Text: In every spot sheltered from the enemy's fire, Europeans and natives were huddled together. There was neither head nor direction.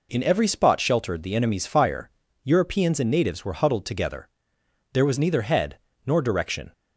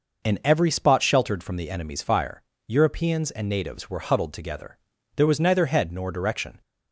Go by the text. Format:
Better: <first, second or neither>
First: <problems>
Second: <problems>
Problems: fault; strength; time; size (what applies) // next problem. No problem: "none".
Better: second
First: skips "from"; at 1.2 s // pauses between "head" and "nor"; slight; at 5.7 s; 0.26 s long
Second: none